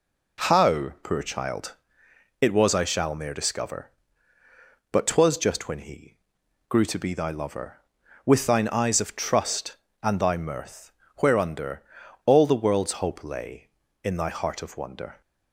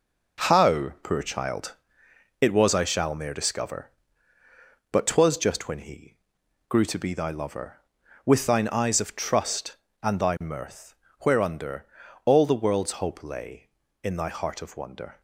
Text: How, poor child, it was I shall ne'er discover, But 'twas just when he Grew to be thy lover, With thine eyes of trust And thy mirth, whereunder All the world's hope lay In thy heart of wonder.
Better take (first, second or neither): first